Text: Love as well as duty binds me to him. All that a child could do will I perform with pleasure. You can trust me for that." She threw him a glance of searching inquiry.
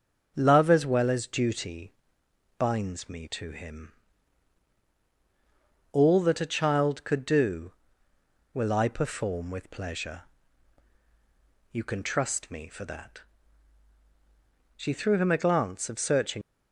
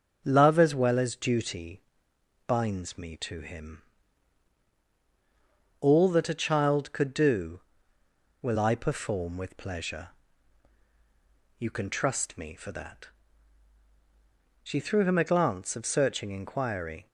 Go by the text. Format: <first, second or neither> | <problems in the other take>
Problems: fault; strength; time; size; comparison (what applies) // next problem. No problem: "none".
second | starts louder than the rest; until 1.3 s; 6.5 dB; also in the second // pauses between "duty" and "binds"; noticeable; at 1.9 s; 0.66 s long; noticeable in the second // stops before "inquiry"; at 16.4 s